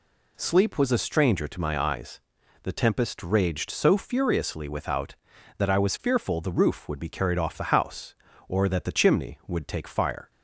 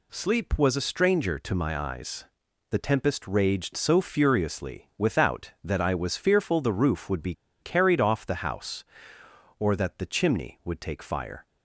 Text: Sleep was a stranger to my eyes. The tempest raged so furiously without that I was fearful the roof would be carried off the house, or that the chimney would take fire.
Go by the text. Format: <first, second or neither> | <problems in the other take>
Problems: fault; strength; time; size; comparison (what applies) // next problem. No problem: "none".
first | pauses between "be" and "carried"; slight; at 7.3 s; 0.28 s long